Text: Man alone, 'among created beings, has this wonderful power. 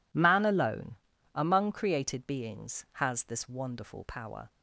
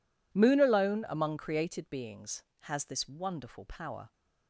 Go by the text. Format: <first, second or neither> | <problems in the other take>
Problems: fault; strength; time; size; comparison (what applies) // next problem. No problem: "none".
first | says "Moon" for "Man"; at 0.3 s